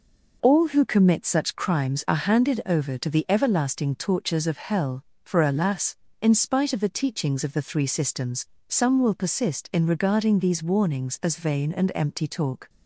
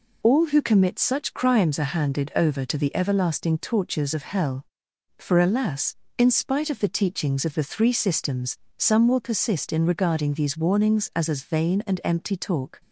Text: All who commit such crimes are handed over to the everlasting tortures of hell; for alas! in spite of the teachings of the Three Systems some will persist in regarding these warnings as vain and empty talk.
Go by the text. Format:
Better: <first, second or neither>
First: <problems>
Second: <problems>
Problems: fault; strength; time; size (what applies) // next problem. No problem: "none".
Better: first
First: pauses between "Systems" and "some"; slight; at 8.4 s; 0.20 s long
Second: pauses between "Systems" and "some"; slight; at 8.5 s; 0.20 s long // says "as" twice; at 11.2 s